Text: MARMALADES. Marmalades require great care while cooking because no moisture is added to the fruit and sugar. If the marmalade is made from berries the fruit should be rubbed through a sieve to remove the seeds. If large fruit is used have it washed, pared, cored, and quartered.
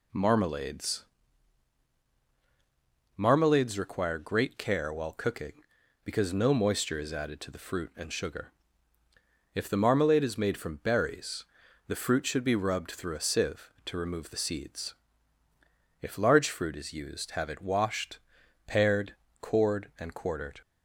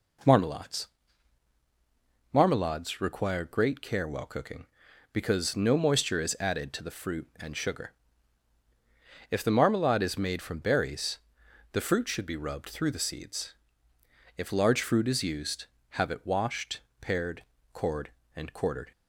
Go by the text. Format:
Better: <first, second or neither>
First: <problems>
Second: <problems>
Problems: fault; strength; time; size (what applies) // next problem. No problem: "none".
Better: first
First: pauses between "berries" and "the"; at 11.4 s; 0.42 s long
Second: pauses between "berries" and "the"; noticeable; at 11.1 s; 0.52 s long // skips "a sieve to remove"; at 12.9 s